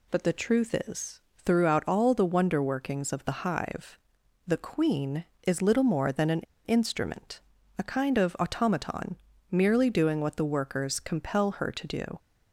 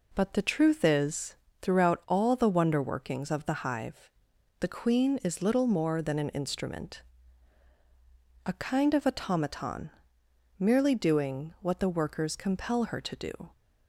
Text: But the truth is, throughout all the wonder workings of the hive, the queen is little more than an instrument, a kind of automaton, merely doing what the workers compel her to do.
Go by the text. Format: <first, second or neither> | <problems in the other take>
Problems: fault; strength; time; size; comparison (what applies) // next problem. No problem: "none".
second | pauses between "an" and "instrument"; slight; at 6.3 s; 0.24 s long